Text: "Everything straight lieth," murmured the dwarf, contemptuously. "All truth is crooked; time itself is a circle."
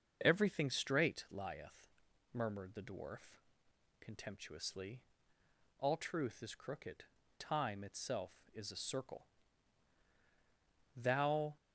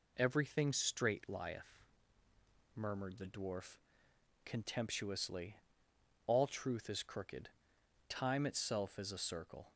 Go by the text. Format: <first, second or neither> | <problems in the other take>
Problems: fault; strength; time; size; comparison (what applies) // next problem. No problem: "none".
second | starts louder than the rest; until 1.2 s; 6.5 dB // goes on to say "Thou"; noticeable; from 10.9 s on; 0.62 s long